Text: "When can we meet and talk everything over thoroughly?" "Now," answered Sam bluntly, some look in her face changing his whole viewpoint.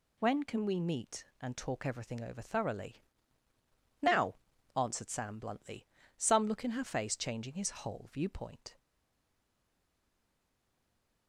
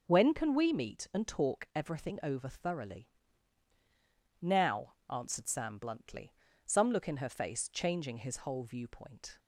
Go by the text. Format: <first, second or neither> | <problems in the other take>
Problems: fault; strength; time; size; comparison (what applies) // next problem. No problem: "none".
second | stays silent after the last word; from 8.7 s on; 2.5 s long